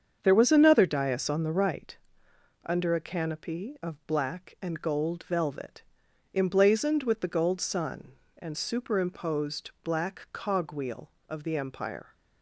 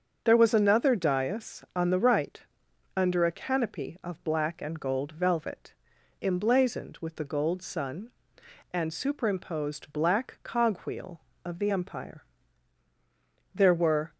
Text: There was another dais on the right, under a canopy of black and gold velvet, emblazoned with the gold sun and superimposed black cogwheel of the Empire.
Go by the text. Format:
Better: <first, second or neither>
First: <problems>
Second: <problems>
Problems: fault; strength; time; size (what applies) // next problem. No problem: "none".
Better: first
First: starts louder than the rest; strong; until 1.2 s; 7.5 dB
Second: starts louder than the rest; until 1.2 s; 6.5 dB // goes on to say "There were"; from 13.5 s on; 0.60 s long